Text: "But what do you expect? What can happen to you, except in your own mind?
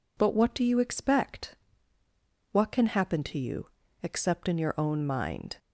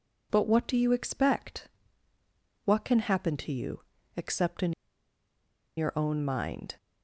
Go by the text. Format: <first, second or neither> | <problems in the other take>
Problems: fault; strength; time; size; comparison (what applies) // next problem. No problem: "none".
first | pauses between "in" and "your"; at 4.7 s; 1.0 s long